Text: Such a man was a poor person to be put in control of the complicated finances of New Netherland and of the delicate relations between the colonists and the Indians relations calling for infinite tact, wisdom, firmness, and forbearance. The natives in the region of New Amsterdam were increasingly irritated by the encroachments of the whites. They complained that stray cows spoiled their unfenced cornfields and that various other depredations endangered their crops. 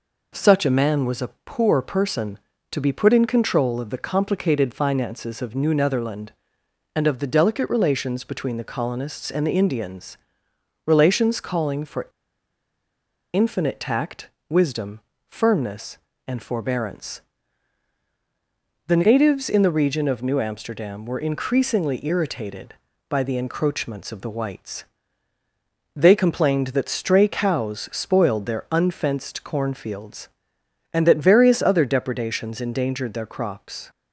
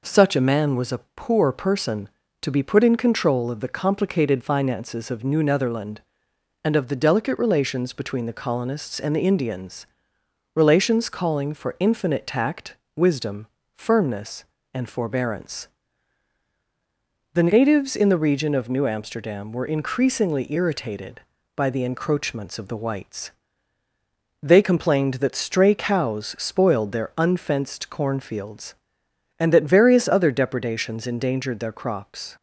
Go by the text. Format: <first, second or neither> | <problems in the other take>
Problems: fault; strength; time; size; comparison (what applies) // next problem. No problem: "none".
second | pauses between "a" and "poor"; slight; at 1.2 s; 0.16 s long; slight in the second // pauses between "Indians" and "relations"; noticeable; at 10.1 s; 0.68 s long; noticeable in the second // pauses between "for" and "infinite"; strong; at 12.0 s; 1.2 s long